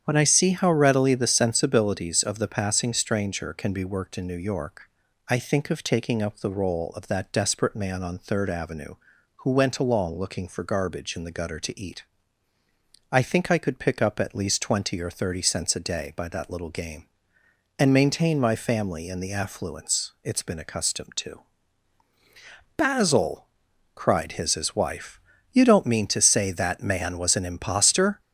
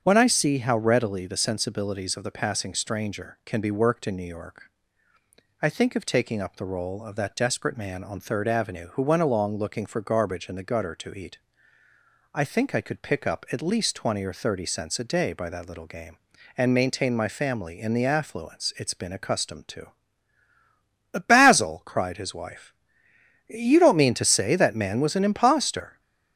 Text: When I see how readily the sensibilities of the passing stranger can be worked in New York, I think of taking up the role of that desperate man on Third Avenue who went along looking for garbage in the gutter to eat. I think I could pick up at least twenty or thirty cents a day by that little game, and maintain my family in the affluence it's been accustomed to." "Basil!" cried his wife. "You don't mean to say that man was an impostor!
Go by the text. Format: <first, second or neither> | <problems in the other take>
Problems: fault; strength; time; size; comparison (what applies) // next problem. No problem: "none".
second | starts louder than the rest; strong; until 1.0 s; 8.5 dB; strong in the second // says "his" twice; at 24.5 s